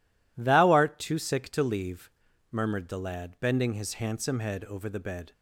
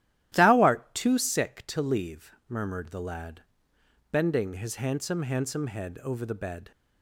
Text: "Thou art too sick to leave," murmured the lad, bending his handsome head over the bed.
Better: first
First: none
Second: starts louder than the rest; strong; until 1.3 s; 13 dB // says "handsome" twice; at 5.2 s

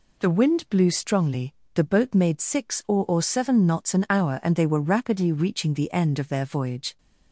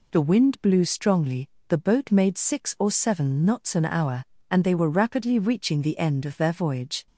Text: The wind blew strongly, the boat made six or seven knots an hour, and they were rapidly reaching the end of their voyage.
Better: second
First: says "or" twice; at 3.0 s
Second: none

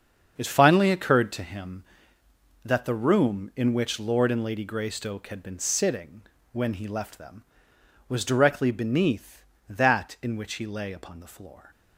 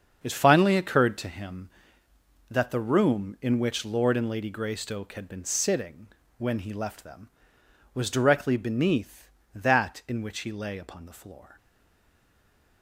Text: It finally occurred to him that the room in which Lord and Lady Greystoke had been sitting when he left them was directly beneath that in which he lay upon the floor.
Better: first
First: starts louder than the rest; strong; until 1.4 s; 7 dB // pauses between "sitting" and "when"; slight; at 6.2 s; 0.30 s long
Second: starts louder than the rest; strong; until 1.2 s; 7 dB // pauses between "sitting" and "when"; slight; at 6.0 s; 0.30 s long // stays silent after the last word; noticeable; from 11.5 s on; 1.3 s long

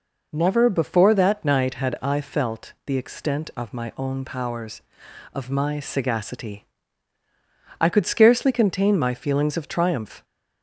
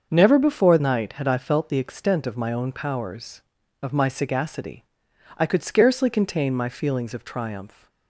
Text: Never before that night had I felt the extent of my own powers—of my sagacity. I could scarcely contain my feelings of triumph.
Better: first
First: none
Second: starts louder than the rest; until 1.1 s; 6.5 dB // skips "that"; at 0.7 s

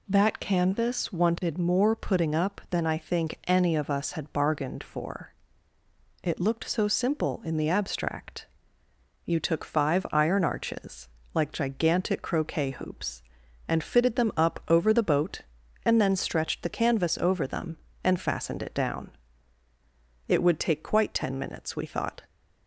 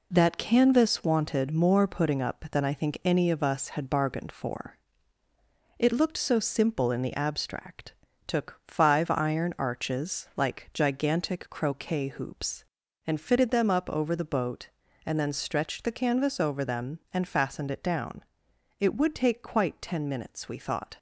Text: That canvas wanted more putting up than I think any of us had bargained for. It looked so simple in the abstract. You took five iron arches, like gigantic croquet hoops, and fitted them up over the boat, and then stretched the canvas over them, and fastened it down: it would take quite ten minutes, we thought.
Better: first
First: none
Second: skips "You"; at 8.1 s

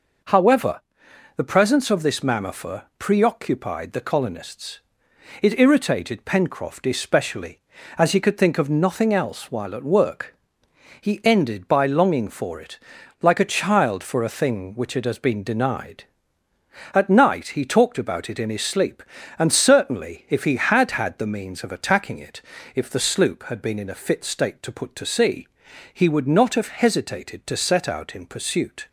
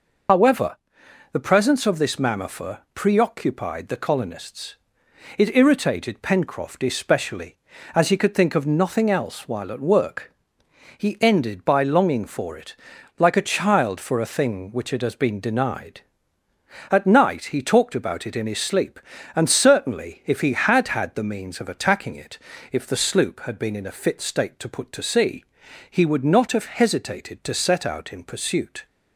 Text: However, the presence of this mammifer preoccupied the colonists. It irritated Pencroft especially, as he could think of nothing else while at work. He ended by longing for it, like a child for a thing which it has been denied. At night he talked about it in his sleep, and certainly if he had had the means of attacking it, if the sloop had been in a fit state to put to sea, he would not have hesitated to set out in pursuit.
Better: first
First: pauses between "mammifer" and "preoccupied"; slight; at 2.8 s; 0.16 s long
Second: loses the start of "However"; at 0.2 s; 90 ms // pauses between "mammifer" and "preoccupied"; slight; at 2.7 s; 0.16 s long

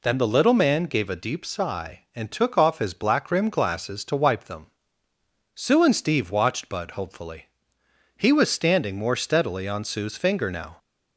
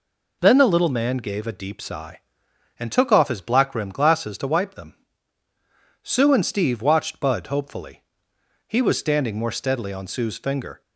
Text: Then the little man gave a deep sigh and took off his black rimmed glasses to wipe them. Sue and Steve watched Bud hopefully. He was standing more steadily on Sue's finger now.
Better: first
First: none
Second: stops before "now"; at 10.8 s

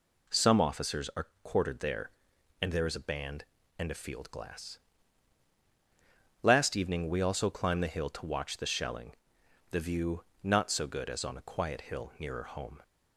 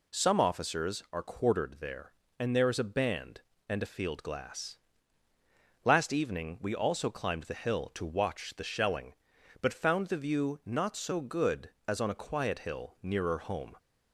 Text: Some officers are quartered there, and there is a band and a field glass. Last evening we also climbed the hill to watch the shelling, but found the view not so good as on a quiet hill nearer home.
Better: second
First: pauses between "are" and "quartered"; slight; at 1.2 s; 0.16 s long // skips "but found"; at 9.4 s // pauses between "view" and "not"; slight; at 10.2 s; 0.20 s long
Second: none

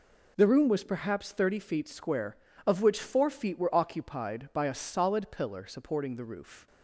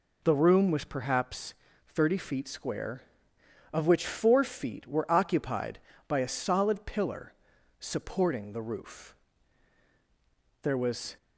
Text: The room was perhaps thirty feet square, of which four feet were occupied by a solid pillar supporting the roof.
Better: first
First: none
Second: pauses between "perhaps" and "thirty"; slight; at 1.5 s; 0.32 s long // pauses between "pillar" and "supporting"; noticeable; at 7.3 s; 0.46 s long // goes on to say "There was"; from 10.6 s on; 0.54 s long

